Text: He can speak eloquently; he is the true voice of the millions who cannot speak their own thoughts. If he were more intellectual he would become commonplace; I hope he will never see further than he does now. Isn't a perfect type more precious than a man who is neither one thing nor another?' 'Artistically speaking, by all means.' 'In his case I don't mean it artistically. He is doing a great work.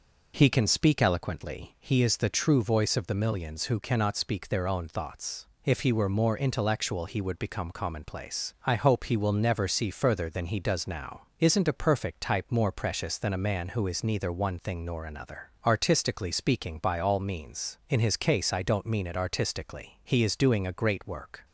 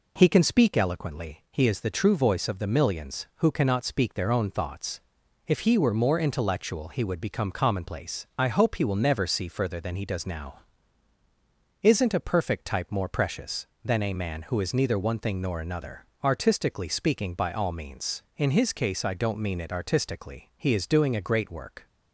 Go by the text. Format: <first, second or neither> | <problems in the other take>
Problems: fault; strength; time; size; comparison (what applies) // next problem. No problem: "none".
neither | none